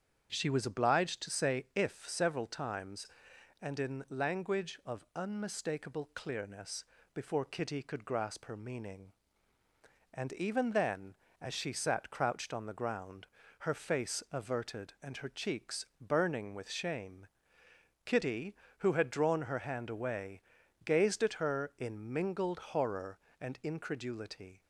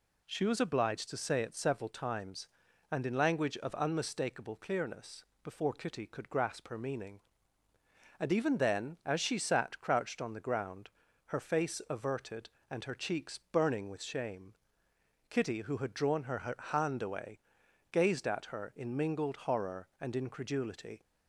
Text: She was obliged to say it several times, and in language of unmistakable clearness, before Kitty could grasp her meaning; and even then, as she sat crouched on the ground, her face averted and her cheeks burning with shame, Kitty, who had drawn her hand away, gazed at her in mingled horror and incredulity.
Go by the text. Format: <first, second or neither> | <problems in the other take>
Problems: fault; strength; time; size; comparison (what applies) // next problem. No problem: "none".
second | starts louder than the rest; strong; until 1.3 s; 8 dB // says "if" for "it"; at 1.7 s